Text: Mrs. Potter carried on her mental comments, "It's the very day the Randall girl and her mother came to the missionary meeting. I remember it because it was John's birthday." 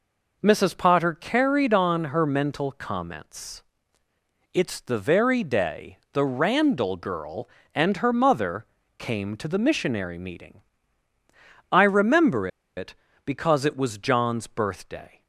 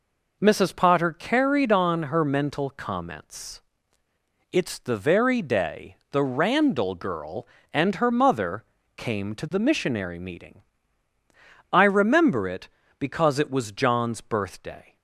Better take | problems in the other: second | pauses between "day" and "the"; slight; at 5.9 s; 0.16 s long; slight in the second // pauses between "mother" and "came"; slight; at 8.6 s; 0.34 s long; slight in the second // pauses between "remember" and "it"; slight; at 12.4 s; 0.29 s long

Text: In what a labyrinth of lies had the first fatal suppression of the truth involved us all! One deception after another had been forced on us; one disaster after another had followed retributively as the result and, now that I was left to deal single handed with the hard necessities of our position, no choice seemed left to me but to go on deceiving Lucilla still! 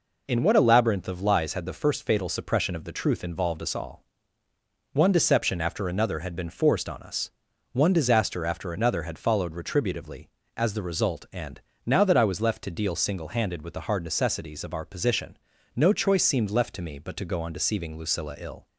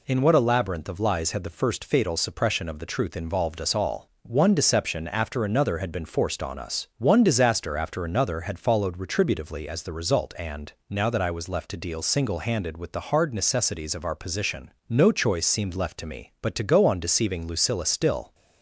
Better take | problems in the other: second | says "ill" for "still"; at 18.3 s

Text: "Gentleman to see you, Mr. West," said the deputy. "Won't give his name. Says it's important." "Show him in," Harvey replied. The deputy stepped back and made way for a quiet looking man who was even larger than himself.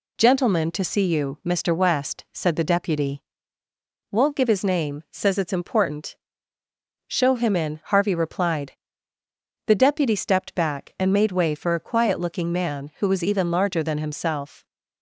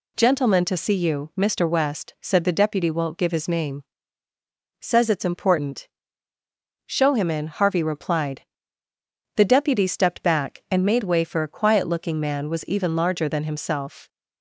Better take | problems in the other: first | skips "who"; at 12.4 s

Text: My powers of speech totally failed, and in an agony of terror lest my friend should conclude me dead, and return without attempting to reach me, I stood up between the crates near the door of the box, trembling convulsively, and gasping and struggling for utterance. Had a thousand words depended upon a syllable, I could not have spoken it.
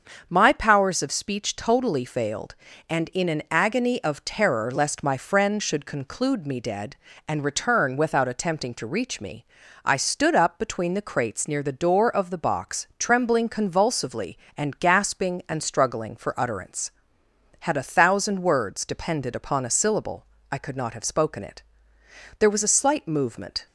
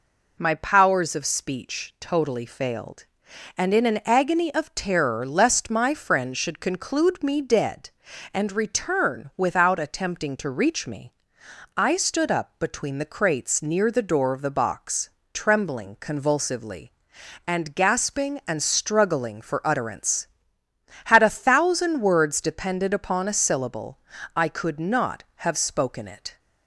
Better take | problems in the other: second | starts louder than the rest; until 1.2 s; 6.5 dB // goes on to say "There was a slight movement"; noticeable; from 22.3 s on; 1.2 s long

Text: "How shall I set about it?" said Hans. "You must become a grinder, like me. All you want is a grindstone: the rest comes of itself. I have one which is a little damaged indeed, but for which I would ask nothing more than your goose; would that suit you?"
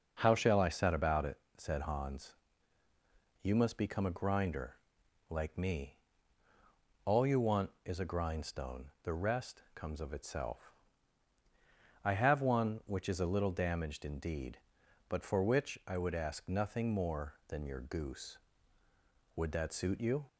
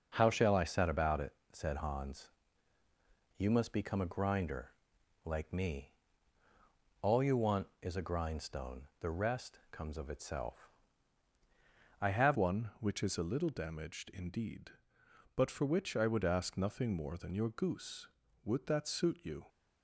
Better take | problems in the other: first | changes voice at "one"; from 12.3 s on; 7.1 s long

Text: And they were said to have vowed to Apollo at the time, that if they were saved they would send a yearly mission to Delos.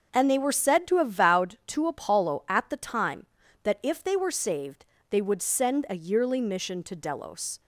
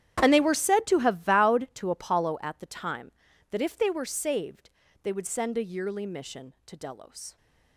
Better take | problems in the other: first | gets quieter; strong; throughout; 17.5 dB // pauses between "saved" and "they"; slight; at 4.6 s; 0.33 s long; slight in the first

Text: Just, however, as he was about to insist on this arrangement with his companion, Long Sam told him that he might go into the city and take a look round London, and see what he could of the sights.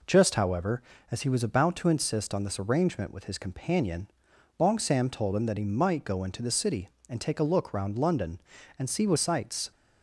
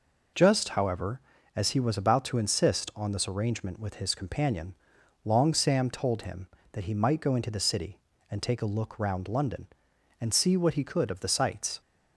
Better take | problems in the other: second | skips "he could of the"; at 9.1 s

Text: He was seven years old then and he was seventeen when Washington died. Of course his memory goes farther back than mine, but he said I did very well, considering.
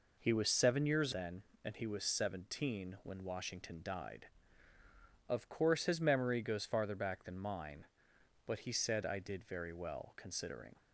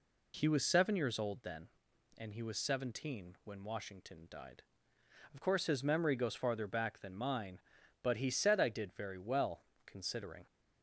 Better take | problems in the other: second | skips "old"; at 1.1 s

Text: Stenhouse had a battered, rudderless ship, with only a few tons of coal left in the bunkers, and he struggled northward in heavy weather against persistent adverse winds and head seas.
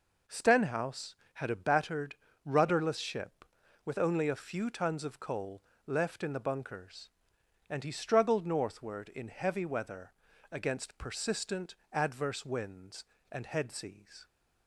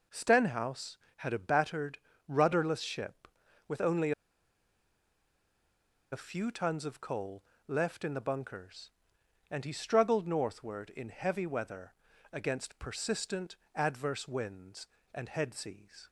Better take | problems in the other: first | pauses between "only" and "a"; strong; at 4.1 s; 2.0 s long // pauses between "coal" and "left"; slight; at 7.4 s; 0.24 s long; slight in the first // pauses between "weather" and "against"; at 11.9 s; 0.38 s long; also in the first // pauses between "persistent" and "adverse"; slight; at 13.5 s; 0.20 s long; slight in the first

